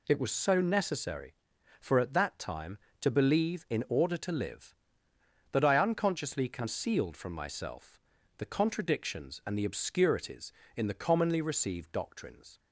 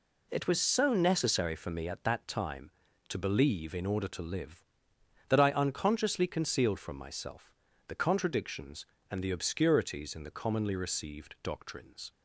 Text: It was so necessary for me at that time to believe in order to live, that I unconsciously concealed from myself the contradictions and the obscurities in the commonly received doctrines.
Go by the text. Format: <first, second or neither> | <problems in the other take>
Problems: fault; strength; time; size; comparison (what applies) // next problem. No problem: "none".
second | skips "me"; at 1.9 s // pauses between "myself" and "the"; at 8.0 s; 0.38 s long; slight in the second